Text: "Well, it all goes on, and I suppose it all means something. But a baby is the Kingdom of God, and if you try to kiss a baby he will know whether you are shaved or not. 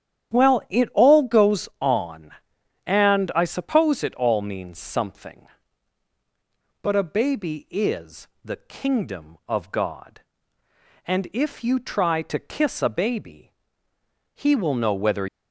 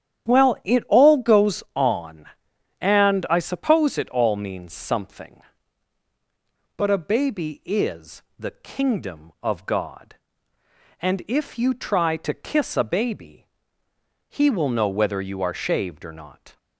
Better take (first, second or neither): second